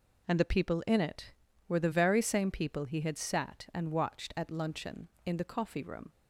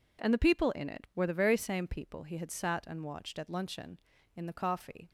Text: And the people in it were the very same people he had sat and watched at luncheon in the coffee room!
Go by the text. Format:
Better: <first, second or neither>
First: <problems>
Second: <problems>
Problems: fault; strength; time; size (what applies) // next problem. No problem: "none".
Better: first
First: none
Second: stops before "room"; at 5.0 s